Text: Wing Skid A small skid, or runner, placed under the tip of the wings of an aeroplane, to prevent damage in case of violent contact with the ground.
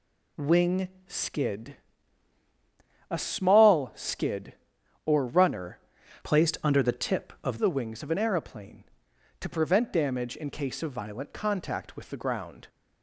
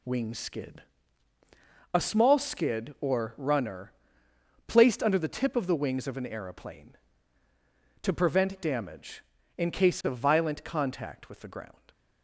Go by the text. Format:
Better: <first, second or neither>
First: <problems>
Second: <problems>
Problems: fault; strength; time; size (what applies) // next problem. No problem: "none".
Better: second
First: pauses between "Wing" and "Skid"; slight; at 0.8 s; 0.18 s long // pauses between "Skid" and "A"; strong; at 1.7 s; 1.3 s long // changes voice from "placed" to "of"; from 6.2 to 7.5 s; 1.3 s long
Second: pauses between "Skid" and "A"; at 0.8 s; 1.1 s long